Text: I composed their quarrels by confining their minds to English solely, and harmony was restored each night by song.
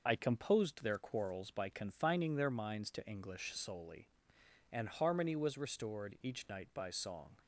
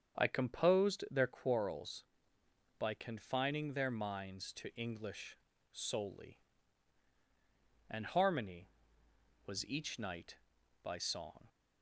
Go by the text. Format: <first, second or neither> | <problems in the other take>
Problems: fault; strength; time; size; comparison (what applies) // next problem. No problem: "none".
first | starts louder than the rest; strong; until 1.2 s; 7.5 dB // pauses between "English" and "solely"; slight; at 5.3 s; 0.36 s long // skips "restored"; at 9.6 s